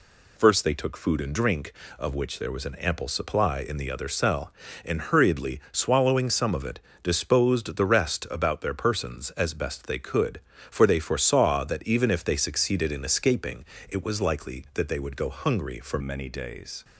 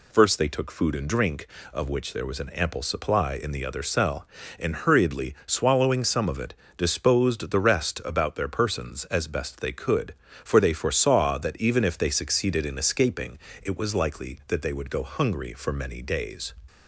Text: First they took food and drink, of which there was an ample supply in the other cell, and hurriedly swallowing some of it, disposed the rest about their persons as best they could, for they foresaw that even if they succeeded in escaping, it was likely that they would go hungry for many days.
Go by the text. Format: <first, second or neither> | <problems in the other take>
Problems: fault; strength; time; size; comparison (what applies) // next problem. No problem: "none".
second | changes voice at "many"; from 16.0 s on; 0.8 s long